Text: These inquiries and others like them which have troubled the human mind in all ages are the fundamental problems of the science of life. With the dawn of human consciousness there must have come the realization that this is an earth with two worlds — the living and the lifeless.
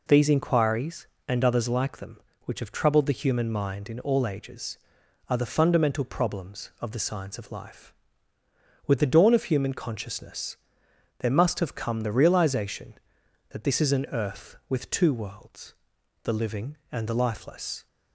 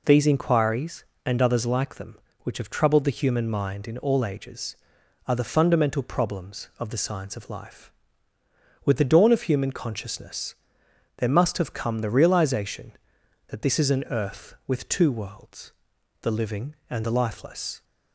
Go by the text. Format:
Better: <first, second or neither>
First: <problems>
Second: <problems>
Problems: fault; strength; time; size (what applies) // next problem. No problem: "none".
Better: neither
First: pauses between "consciousness" and "there"; noticeable; at 10.5 s; 0.64 s long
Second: pauses between "consciousness" and "there"; noticeable; at 10.5 s; 0.64 s long